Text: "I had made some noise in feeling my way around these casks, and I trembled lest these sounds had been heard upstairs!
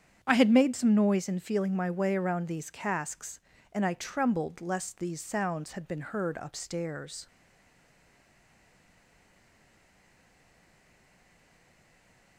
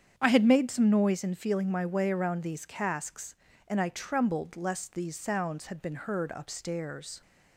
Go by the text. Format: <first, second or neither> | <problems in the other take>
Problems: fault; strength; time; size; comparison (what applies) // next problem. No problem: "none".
second | starts louder than the rest; strong; until 1.2 s; 8 dB; strong in the second // stays silent after the last word; strong; from 7.2 s on; 5.1 s long